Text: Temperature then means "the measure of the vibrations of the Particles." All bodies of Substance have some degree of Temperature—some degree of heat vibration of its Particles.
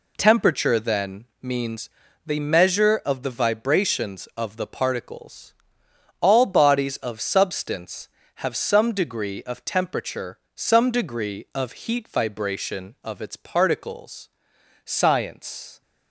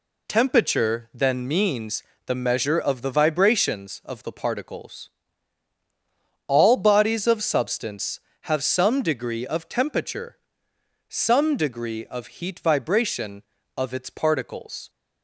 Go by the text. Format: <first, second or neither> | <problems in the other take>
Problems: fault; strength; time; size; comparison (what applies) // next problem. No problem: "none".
second | pauses between "then" and "means"; slight; at 1.2 s; 0.16 s long // pauses between "means" and "the"; slight; at 1.8 s; 0.34 s long; slight in the second // goes on to say "Science"; noticeable; from 14.8 s on; 0.96 s long